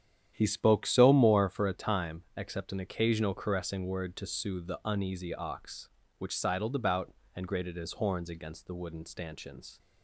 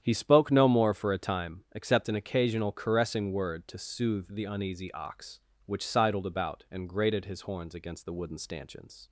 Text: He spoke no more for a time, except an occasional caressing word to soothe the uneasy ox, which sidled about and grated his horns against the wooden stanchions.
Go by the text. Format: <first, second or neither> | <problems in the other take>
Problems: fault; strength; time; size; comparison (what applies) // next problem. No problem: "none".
second | starts louder than the rest; strong; until 1.3 s; 10 dB; strong in the second // says "so" for "no"; at 0.8 s